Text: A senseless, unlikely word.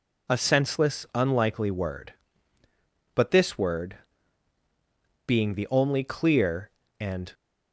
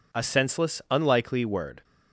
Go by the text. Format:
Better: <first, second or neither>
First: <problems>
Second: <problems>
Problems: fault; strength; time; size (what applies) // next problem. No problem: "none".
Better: second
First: goes on to say "But this word being the only clear and"; strong; from 3.1 s on; 4.1 s long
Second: none